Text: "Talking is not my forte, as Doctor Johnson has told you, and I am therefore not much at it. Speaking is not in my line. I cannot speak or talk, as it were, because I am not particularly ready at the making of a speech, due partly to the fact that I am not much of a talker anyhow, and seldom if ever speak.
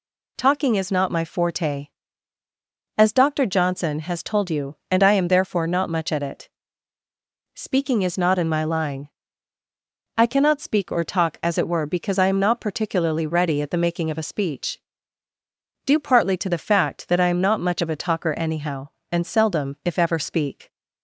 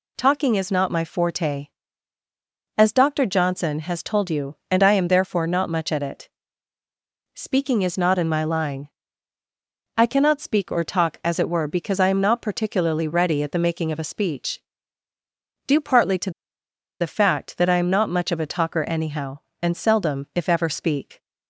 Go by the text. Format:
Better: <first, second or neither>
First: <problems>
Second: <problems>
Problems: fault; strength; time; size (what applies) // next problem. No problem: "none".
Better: first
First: none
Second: pauses between "to" and "the"; noticeable; at 16.3 s; 0.69 s long